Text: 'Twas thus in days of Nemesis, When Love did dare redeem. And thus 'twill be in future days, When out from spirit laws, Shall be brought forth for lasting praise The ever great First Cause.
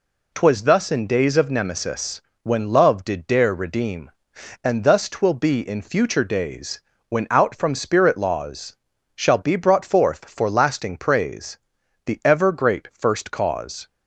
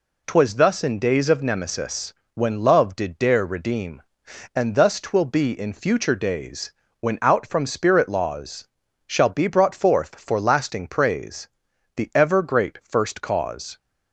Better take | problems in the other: neither | pauses between "praise" and "The"; noticeable; the same in both

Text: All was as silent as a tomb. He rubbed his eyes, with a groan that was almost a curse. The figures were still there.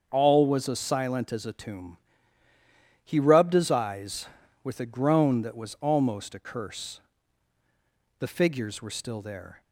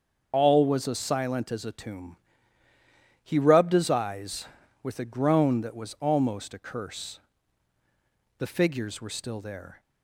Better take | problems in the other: first | loses the start of "All"; at 0.3 s; 40 ms // starts louder than the rest; until 1.3 s; 7 dB; also in the first

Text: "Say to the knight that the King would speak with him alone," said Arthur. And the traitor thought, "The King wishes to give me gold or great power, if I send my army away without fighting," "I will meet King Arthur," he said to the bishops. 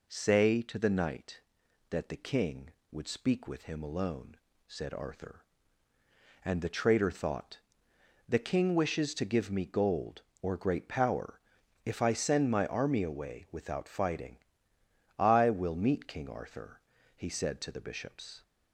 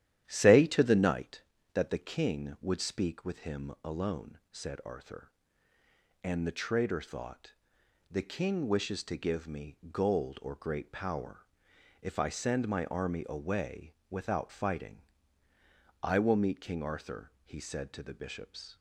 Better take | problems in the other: first | starts louder than the rest; strong; until 1.4 s; 11.5 dB // pauses between "me" and "gold"; slight; at 9.7 s; 0.16 s long // pauses between "away" and "without"; slight; at 13.9 s; 0.16 s long

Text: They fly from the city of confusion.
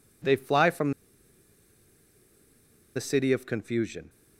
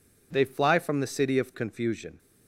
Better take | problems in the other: second | pauses between "from" and "the"; strong; at 0.9 s; 2.0 s long

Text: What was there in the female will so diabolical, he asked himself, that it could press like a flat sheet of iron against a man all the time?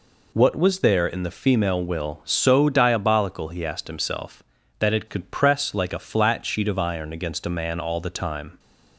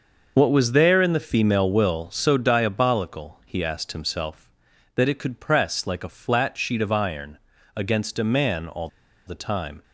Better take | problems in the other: first | starts louder than the rest; noticeable; until 1.3 s; 6 dB // pauses between "iron" and "against"; slight; at 7.3 s; 0.36 s long // pauses between "all" and "the"; at 8.8 s; 0.36 s long

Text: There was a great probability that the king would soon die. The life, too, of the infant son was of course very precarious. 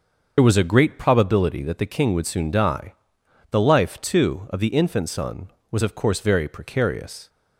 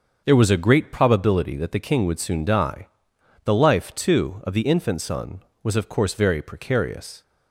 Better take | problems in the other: second | loses the start of "There"; at 0.3 s; 60 ms // starts louder than the rest; until 1.3 s; 6.5 dB; also in the second

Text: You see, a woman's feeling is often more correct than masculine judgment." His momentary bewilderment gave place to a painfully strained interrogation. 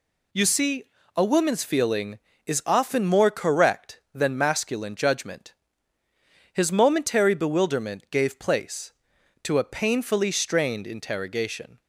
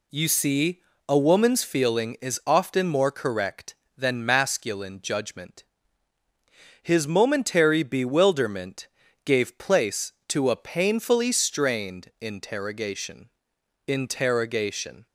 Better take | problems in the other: first | pauses between "bewilderment" and "gave"; at 8.8 s; 0.38 s long // says "interrogation" twice; at 13.8 s

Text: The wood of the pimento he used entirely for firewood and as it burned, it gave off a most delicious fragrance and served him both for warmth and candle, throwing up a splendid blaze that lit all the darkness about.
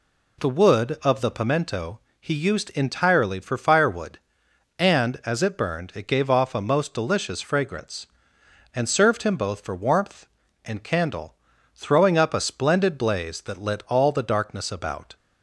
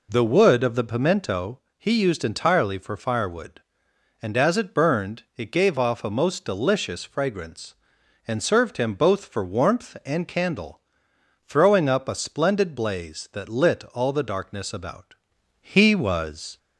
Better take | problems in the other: first | pauses between "pimento" and "he"; slight; at 1.5 s; 0.18 s long; slight in the first // goes on to say "He was"; noticeable; from 15.6 s on; 0.96 s long

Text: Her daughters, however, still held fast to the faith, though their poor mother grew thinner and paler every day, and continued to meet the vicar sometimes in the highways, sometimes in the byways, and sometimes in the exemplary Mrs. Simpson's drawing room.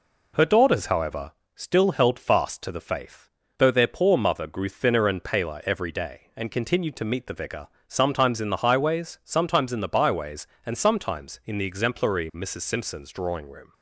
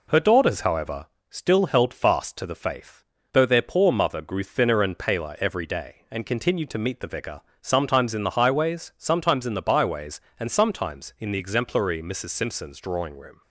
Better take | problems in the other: neither | pauses between "vicar" and "sometimes"; slight; the same in both

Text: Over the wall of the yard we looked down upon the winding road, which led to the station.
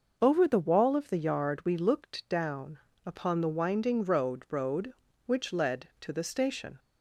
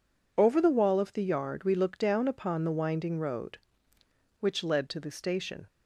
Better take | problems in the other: second | pauses between "down" and "upon"; slight; at 2.7 s; 0.26 s long // says "road" twice; at 4.4 s

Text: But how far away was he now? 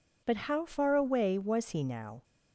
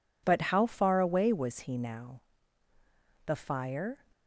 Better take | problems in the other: first | goes on to say "The fire"; noticeable; from 3.2 s on; 0.78 s long

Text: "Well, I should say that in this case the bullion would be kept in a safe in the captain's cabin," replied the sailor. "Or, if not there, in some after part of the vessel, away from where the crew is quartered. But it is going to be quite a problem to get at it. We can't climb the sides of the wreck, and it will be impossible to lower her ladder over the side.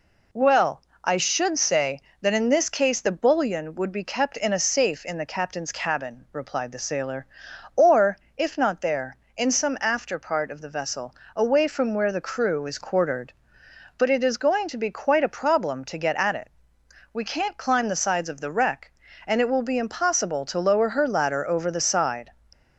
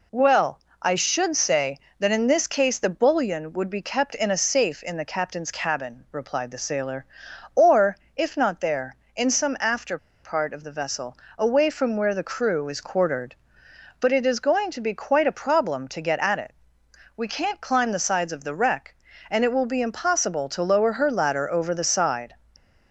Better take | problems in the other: first | pauses between "after" and "part"; slight; at 9.9 s; 0.23 s long

